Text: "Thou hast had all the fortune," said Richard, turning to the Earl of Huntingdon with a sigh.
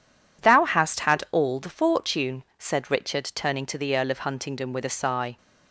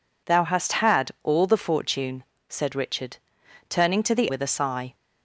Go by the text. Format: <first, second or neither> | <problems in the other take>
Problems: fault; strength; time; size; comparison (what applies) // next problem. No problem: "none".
first | skips "Earl of Huntingdon"; at 4.2 s